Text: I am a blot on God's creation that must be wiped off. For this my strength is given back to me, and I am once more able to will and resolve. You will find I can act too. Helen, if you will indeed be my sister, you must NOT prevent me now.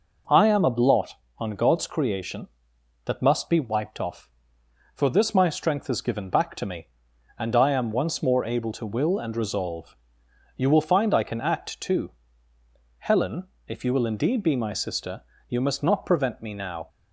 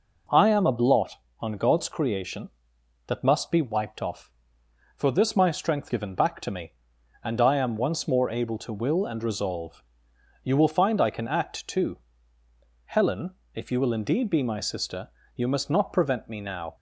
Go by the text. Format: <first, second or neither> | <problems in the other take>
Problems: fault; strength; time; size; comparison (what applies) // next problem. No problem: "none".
first | skips "is"; at 5.8 s